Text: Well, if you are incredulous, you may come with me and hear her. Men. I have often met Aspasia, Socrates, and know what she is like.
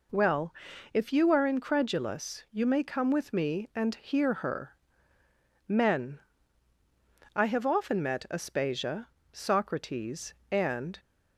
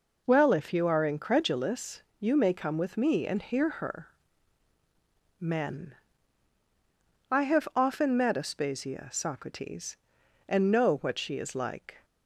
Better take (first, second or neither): second